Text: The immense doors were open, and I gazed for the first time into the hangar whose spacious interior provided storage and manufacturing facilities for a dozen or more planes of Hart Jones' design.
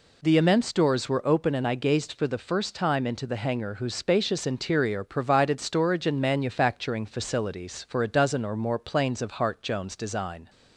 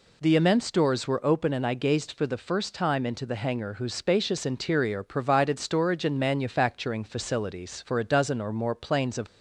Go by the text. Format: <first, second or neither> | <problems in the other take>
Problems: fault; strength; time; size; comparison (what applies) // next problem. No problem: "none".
first | stops before "Hart Jones design"; at 9.2 s